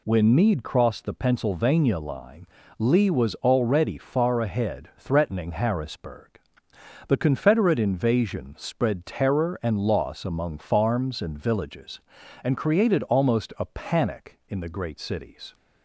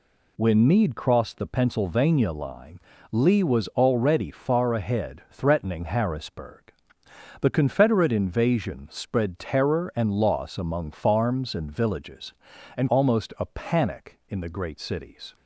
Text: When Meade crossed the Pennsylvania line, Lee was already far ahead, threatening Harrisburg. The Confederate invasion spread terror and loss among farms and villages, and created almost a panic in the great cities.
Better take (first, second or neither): first